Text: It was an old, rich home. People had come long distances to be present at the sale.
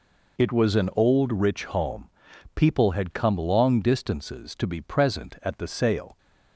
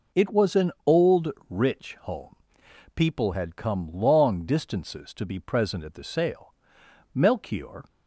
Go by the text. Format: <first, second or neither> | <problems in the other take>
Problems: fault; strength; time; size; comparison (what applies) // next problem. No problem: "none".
first | goes on to say "Melchior"; noticeable; from 7.1 s on; 0.70 s long